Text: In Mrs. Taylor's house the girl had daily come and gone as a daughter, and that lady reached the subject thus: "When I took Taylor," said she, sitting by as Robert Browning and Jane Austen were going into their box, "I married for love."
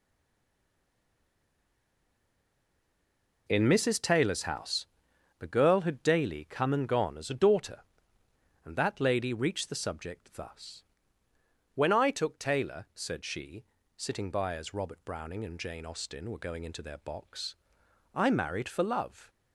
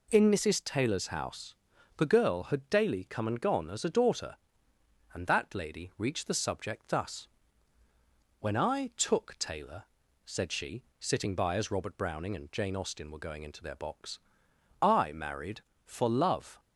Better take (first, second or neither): second